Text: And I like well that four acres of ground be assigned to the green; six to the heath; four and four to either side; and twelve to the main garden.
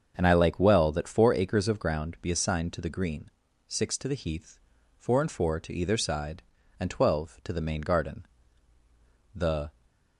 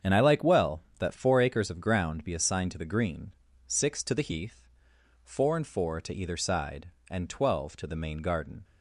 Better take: second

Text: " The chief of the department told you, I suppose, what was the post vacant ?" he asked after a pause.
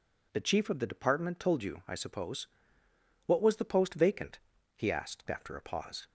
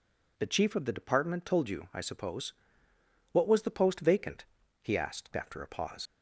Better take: first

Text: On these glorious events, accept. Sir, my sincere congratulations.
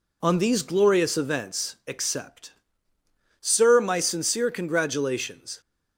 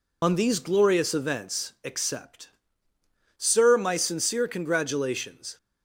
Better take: first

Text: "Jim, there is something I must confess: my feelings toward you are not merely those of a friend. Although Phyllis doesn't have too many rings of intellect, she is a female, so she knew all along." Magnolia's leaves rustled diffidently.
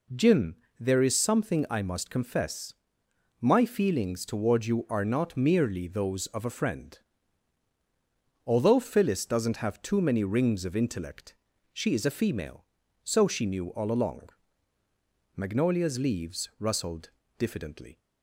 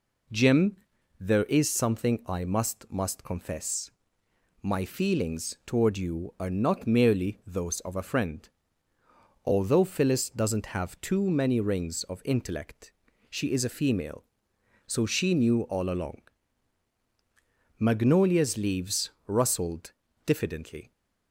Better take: first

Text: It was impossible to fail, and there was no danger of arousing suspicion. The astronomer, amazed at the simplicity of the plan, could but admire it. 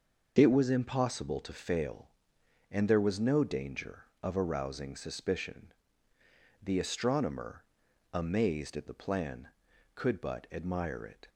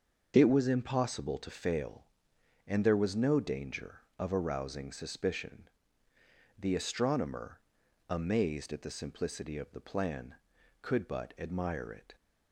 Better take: second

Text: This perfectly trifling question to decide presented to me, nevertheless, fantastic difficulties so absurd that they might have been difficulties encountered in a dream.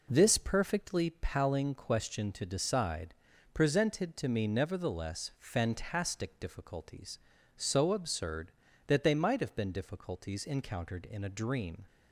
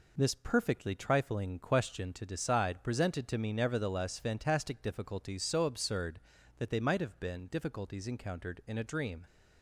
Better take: second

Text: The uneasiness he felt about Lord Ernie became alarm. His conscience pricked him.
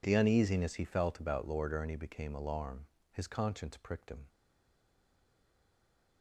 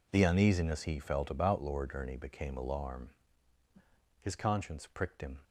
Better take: second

